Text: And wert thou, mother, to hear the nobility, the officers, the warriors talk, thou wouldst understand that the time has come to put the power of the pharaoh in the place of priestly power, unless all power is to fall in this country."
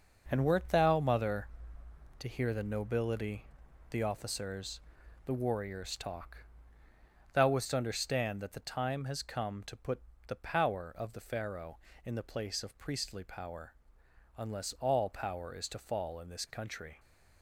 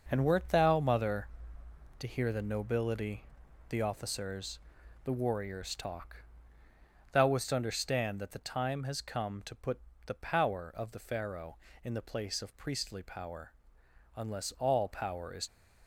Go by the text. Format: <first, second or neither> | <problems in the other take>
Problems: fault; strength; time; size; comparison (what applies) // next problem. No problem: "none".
first | pauses between "put" and "the"; slight; at 9.7 s; 0.26 s long; slight in the first // stops before "to fall in this country"; at 15.4 s